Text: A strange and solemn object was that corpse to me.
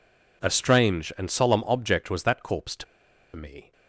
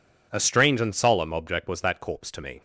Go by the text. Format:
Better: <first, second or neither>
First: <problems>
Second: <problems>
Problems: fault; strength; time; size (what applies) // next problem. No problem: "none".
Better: second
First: pauses between "to" and "me"; noticeable; at 2.8 s; 0.50 s long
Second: none